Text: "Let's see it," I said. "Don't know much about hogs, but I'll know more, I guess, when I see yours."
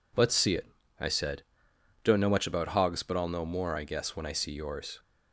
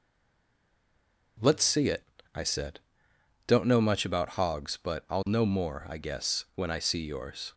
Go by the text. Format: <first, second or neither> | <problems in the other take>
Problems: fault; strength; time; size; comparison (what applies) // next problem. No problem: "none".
first | stays silent before the first word; noticeable; until 1.3 s; 1.3 s long